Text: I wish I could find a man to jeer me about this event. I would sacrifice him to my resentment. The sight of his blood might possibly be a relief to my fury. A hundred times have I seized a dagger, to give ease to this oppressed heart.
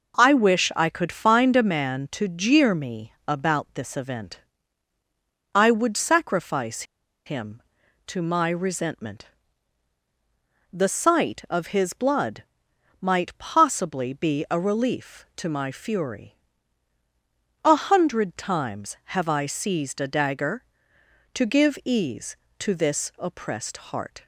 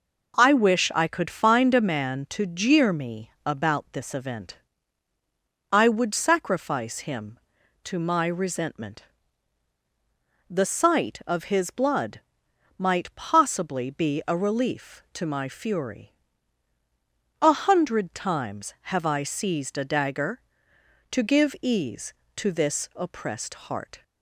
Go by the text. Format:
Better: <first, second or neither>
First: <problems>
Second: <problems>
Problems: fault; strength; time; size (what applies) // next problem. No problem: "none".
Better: second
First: pauses between "me" and "about"; slight; at 3.1 s; 0.16 s long // pauses between "sacrifice" and "him"; at 6.8 s; 0.42 s long // pauses between "blood" and "might"; noticeable; at 12.4 s; 0.58 s long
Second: pauses between "me" and "about"; slight; at 3.2 s; 0.16 s long // pauses between "blood" and "might"; noticeable; at 12.2 s; 0.58 s long